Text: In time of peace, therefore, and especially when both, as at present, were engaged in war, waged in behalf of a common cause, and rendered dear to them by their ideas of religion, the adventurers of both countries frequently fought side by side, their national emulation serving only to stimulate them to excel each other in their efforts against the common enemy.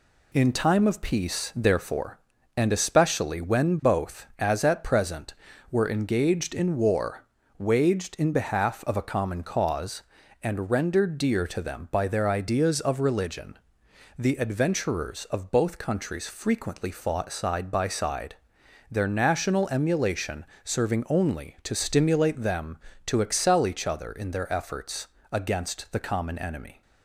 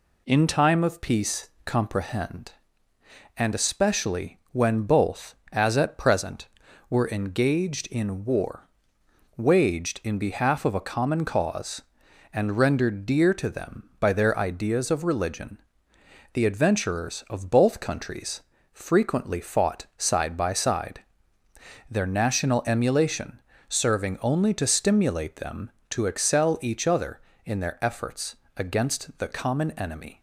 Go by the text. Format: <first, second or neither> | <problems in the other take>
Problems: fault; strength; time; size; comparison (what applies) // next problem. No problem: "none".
first | says "comprehend" for "therefore"; at 1.6 s // pauses between "especially" and "when"; slight; at 4.3 s; 0.16 s long // pauses between "countries" and "frequently"; slight; at 18.3 s; 0.32 s long // pauses between "emulation" and "serving"; slight; at 23.4 s; 0.26 s long; slight in the first // pauses between "efforts" and "against"; slight; at 28.3 s; 0.18 s long; slight in the first